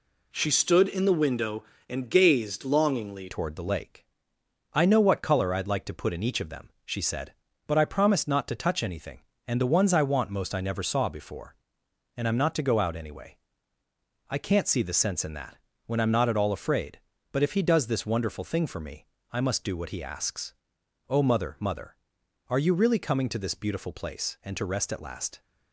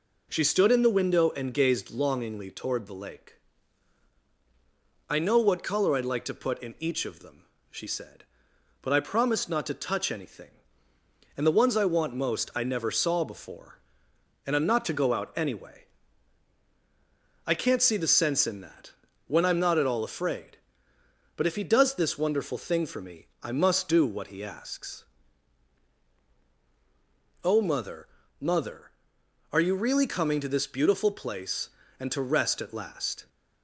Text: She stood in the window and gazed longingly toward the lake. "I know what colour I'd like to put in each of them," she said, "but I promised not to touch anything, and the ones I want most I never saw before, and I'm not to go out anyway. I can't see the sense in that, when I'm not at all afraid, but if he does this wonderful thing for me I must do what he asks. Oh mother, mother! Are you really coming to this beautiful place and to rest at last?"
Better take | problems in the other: second | changes voice at "toward"; from 3.2 s on; 22.2 s long // pauses between "me" and "I"; slight; at 19.0 s; 0.26 s long

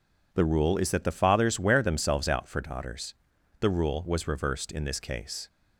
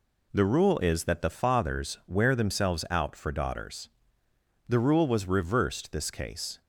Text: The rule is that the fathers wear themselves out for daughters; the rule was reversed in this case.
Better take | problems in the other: first | skips "in"; at 5.9 s

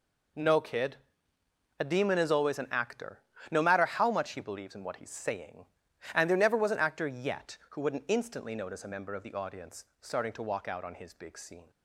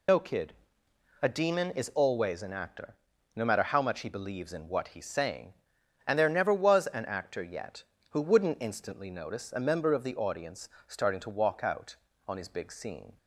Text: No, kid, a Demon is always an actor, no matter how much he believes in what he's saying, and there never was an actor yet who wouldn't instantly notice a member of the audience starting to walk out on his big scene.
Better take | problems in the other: first | loses the start of "No"; at 0.0 s; 75 ms // pauses between "audience" and "starting"; slight; at 10.6 s; 0.18 s long; slight in the first

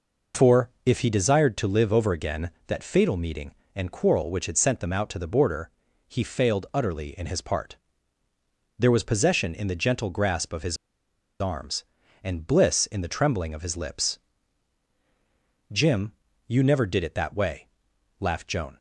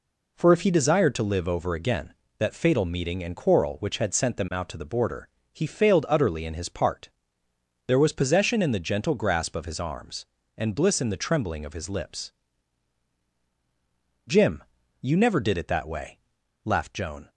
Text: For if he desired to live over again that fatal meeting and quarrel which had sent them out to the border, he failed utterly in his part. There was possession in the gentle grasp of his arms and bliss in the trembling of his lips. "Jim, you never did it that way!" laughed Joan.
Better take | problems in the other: second | pauses between "his" and "arms"; noticeable; at 10.7 s; 0.64 s long

